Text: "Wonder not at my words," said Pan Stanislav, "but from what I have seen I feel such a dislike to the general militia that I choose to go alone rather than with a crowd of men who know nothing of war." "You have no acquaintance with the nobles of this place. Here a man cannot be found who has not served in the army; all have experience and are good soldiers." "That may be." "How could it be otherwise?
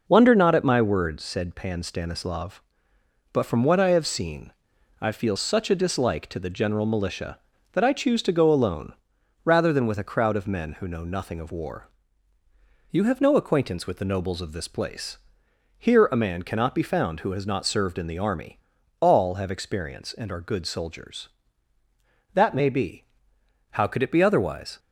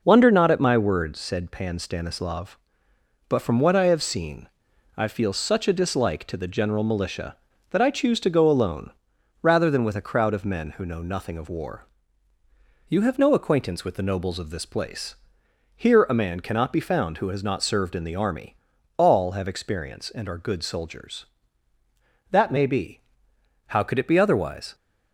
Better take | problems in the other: neither | pauses between "seen" and "I"; noticeable; the same in both // pauses between "alone" and "rather"; noticeable; the same in both

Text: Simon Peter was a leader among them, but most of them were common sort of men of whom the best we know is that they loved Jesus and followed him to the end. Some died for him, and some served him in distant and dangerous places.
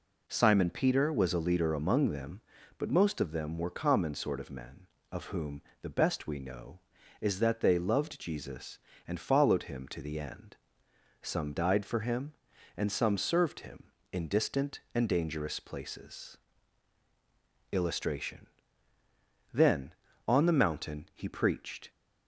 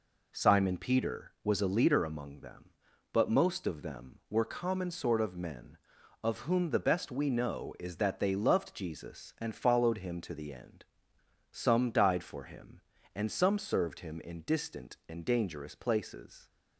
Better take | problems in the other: second | pauses between "whom" and "the"; slight; at 5.6 s; 0.18 s long // goes on to say "Illustration Then on the mountain he preached"; strong; from 17.7 s on; 4.1 s long

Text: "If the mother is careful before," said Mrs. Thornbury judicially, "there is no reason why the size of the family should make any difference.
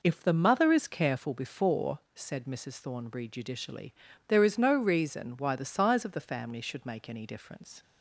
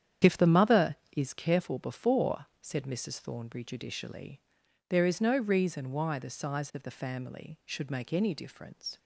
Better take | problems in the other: first | starts louder than the rest; strong; until 1.6 s; 9 dB

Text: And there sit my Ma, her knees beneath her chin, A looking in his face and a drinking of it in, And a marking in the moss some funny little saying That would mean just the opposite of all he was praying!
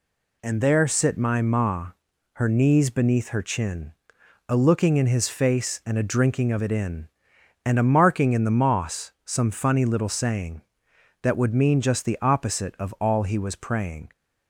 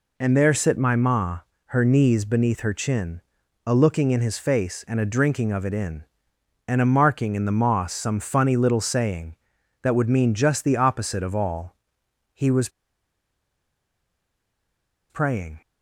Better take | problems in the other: first | pauses between "all" and "he"; noticeable; at 11.7 s; 0.60 s long // pauses between "was" and "praying"; strong; at 12.6 s; 2.4 s long

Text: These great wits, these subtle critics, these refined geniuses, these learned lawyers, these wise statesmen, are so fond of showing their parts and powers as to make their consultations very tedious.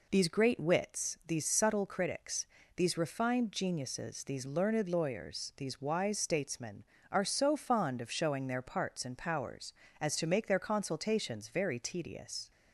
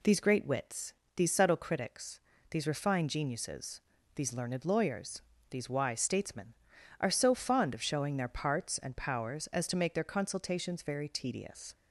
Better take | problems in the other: neither | none

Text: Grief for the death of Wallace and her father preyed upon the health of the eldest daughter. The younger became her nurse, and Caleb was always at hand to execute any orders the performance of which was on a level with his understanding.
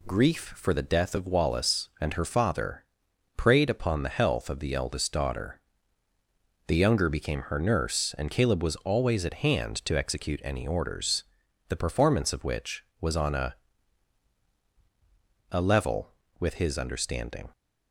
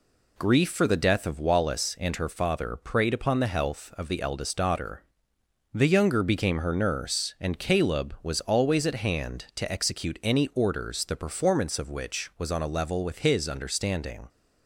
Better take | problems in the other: second | pauses between "father" and "preyed"; noticeable; at 2.8 s; 0.52 s long // pauses between "orders" and "the"; at 11.2 s; 0.44 s long // says "a" twice; at 15.4 s

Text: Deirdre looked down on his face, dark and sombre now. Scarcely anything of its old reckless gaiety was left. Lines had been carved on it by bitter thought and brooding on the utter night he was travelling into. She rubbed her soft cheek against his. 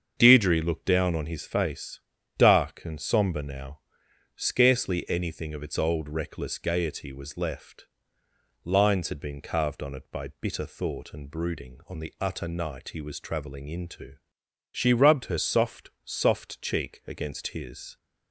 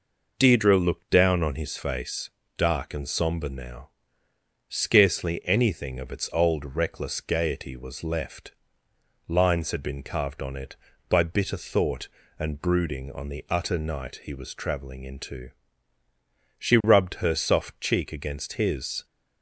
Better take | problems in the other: second | starts louder than the rest; until 1.1 s; 7 dB // says "soft" twice; at 16.0 s

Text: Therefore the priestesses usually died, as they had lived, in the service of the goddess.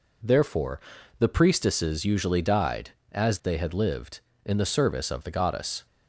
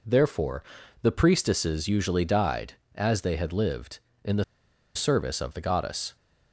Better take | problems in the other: first | pauses between "Therefore" and "the"; at 0.6 s; 0.38 s long; also in the first // pauses between "the" and "service"; noticeable; at 4.4 s; 0.51 s long

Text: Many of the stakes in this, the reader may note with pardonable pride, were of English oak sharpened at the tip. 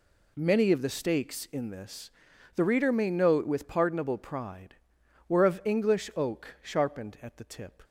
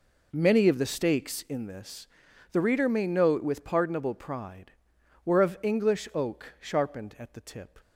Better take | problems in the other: first | starts louder than the rest; noticeable; until 1.6 s; 4.5 dB

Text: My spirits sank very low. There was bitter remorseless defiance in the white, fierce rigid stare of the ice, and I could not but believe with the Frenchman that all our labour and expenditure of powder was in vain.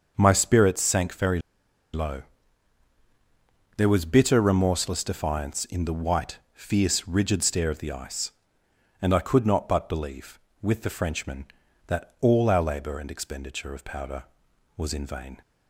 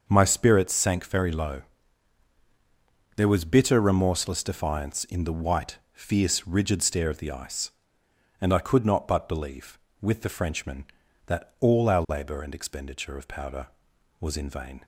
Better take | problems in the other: second | starts louder than the rest; until 1.1 s; 6.5 dB; also in the second // pauses between "very" and "low"; noticeable; at 1.4 s; 0.52 s long

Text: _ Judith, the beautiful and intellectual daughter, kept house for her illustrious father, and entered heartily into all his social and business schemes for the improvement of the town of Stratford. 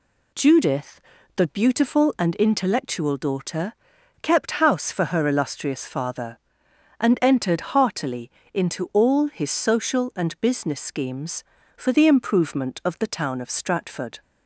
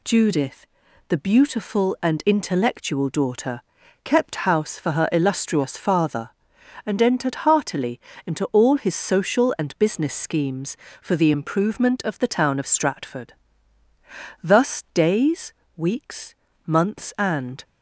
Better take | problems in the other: first | pauses between "heartily" and "into"; slight; at 7.9 s; 0.26 s long; slight in the first // goes on to say "Thus days weeks months and"; strong; from 14.4 s on; 3.2 s long

